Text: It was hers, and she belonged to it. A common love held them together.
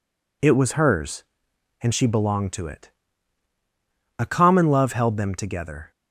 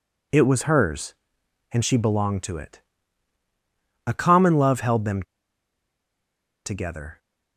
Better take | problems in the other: first | pauses between "them" and "together"; strong; at 5.2 s; 1.4 s long

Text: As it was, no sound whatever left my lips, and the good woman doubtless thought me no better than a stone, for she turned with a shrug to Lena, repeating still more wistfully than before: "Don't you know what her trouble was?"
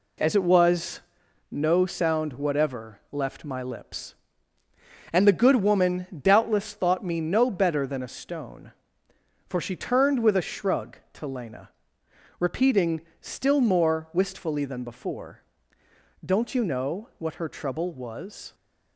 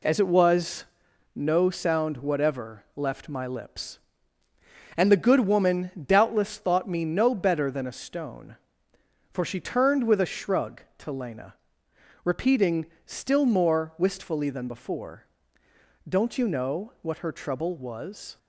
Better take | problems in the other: neither | pauses between "woman" and "doubtless"; slight; the same in both // pauses between "repeating" and "still"; slight; the same in both

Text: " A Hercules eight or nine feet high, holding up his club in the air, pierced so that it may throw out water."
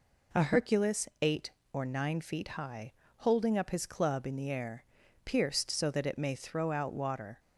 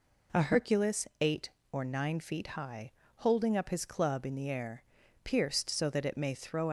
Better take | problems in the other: first | stops before "out water"; at 6.6 s

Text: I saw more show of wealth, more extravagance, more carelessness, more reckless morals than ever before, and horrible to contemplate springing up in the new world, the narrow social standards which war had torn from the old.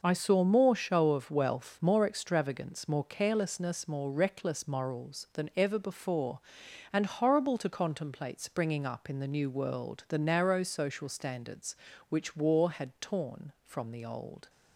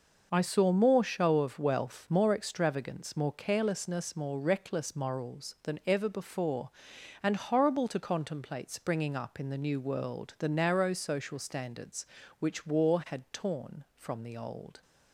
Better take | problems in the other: neither | none

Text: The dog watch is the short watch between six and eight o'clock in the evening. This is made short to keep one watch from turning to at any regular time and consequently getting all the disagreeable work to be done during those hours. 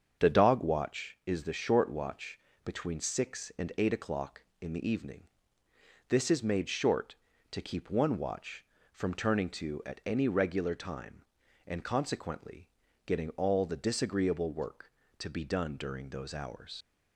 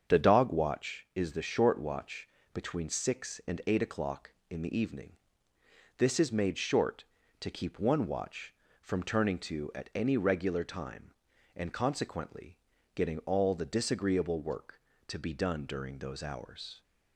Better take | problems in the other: second | starts louder than the rest; until 1.3 s; 7 dB; also in the second // pauses between "watch" and "between"; slight; at 2.3 s; 0.24 s long; slight in the second // pauses between "consequently" and "getting"; at 12.6 s; 0.38 s long; also in the second // leaves "hours" unfinished; at 16.8 s; 130 ms

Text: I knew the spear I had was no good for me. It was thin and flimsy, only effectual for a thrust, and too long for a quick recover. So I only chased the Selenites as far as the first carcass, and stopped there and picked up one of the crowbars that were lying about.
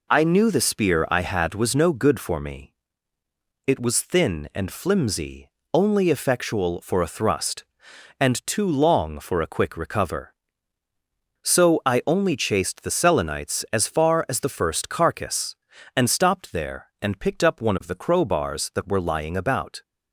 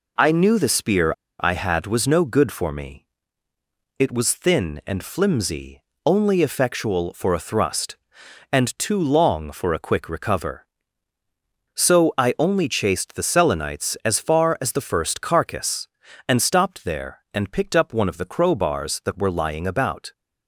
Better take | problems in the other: first | pauses between "spear" and "I"; slight; at 1.1 s; 0.28 s long

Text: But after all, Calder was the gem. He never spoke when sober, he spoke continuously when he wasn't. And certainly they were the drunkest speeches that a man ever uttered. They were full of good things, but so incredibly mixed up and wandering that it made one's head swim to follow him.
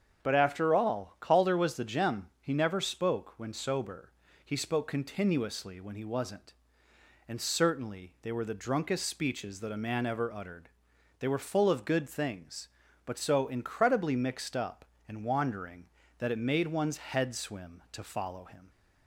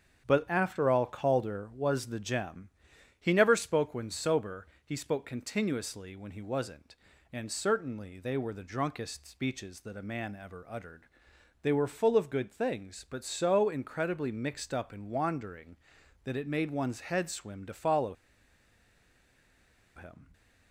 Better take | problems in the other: first | starts louder than the rest; strong; until 1.2 s; 8 dB; strong in the first // pauses between "follow" and "him"; strong; at 18.1 s; 1.8 s long

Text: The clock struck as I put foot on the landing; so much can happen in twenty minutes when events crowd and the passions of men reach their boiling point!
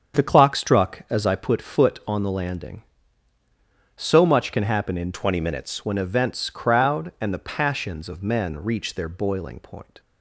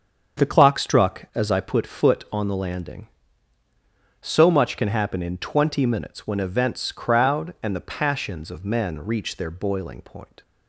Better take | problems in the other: second | starts louder than the rest; strong; until 1.2 s; 7.5 dB; also in the second // changes voice from "twenty" to "minutes"; from 5.1 to 5.8 s; 0.7 s long

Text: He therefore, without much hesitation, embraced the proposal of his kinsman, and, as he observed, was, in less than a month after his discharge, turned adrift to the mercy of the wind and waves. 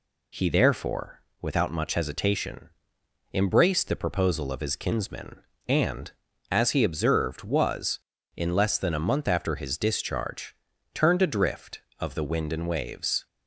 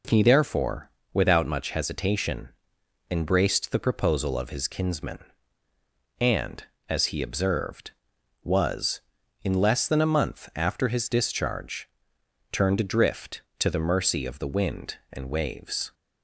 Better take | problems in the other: second | skips "to the mercy"; at 11.9 s

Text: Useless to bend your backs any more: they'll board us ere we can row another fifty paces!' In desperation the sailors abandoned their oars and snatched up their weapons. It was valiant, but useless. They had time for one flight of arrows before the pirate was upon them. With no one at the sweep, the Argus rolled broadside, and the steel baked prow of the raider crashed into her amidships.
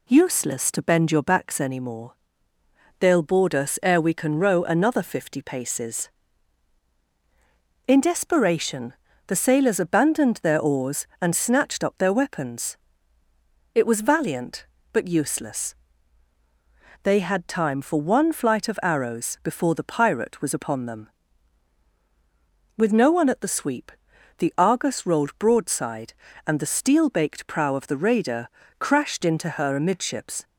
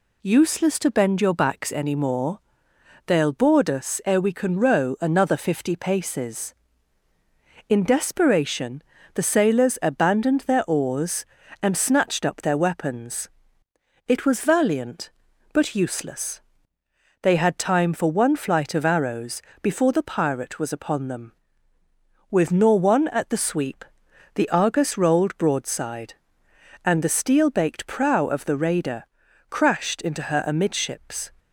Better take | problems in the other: first | pauses between "desperation" and "the"; slight; at 8.8 s; 0.32 s long; slight in the first // pauses between "arrows" and "before"; slight; at 19.4 s; 0.21 s long // says "nor" for "no"; at 22.5 s // pauses between "raider" and "crashed"; noticeable; at 29.0 s; 0.46 s long; slight in the first

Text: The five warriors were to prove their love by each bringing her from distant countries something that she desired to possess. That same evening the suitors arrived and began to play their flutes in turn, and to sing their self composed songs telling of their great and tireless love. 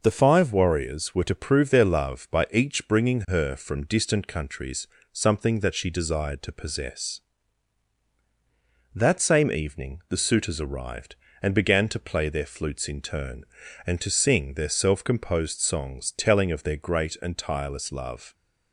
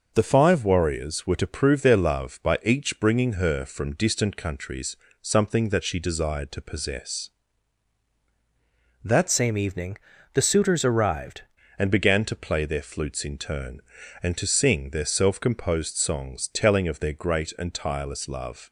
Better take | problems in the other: first | pauses between "countries" and "something"; slight; at 4.9 s; 0.26 s long; slight in the first // changes voice from "same" to "arrived"; from 9.2 to 11.4 s; 2.2 s long // pauses between "evening" and "the"; slight; at 9.9 s; 0.36 s long

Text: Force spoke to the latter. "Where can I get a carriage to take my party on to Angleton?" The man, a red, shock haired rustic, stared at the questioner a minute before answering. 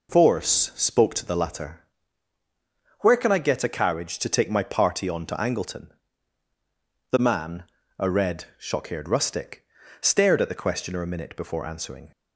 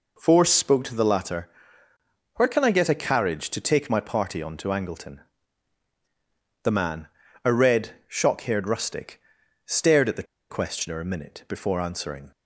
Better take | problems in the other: first | pauses between "the" and "questioner"; slight; at 10.2 s; 0.26 s long

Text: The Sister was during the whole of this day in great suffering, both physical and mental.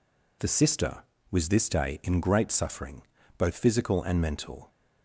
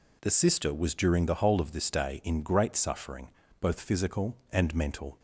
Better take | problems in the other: second | skips "during the whole of"; at 1.4 s

